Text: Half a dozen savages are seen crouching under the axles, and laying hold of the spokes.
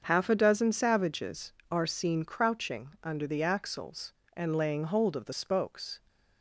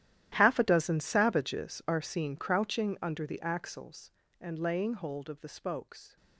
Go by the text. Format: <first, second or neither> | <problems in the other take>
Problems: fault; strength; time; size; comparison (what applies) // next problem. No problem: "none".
first | gets quieter; strong; throughout; 17 dB // starts louder than the rest; strong; until 1.3 s; 13 dB; also in the first